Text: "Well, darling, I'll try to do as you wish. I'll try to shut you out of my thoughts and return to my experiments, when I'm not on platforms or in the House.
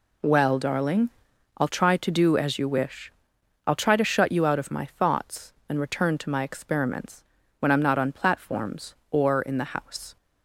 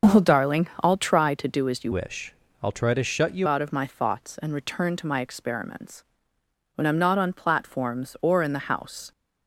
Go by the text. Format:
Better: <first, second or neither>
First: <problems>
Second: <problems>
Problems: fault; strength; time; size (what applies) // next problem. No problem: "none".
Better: first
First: none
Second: starts louder than the rest; until 1.1 s; 6 dB // changes voice from "wish" to "you"; from 1.9 to 3.4 s; 1.5 s long